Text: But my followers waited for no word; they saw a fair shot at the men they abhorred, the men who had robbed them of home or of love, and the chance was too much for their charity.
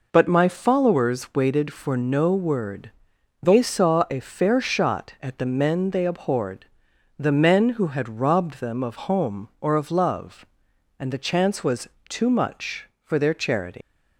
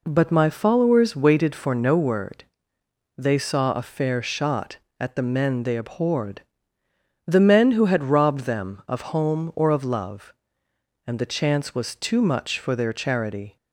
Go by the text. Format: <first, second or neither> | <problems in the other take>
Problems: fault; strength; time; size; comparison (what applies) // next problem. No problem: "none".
second | pauses between "was" and "too"; slight; at 11.8 s; 0.18 s long // leaves "charity" unfinished; at 13.8 s; 110 ms